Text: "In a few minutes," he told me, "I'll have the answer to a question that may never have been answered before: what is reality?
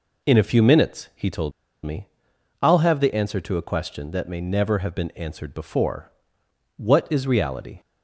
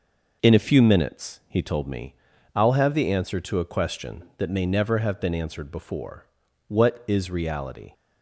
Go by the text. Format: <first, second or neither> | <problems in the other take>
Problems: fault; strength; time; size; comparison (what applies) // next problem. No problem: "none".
second | pauses between "told" and "me"; slight; at 1.5 s; 0.32 s long